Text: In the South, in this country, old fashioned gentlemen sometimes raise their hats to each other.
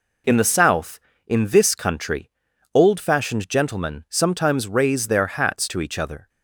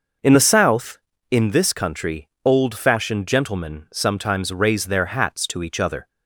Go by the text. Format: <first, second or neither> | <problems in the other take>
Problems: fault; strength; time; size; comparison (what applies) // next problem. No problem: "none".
first | starts louder than the rest; noticeable; until 1.3 s; 5.5 dB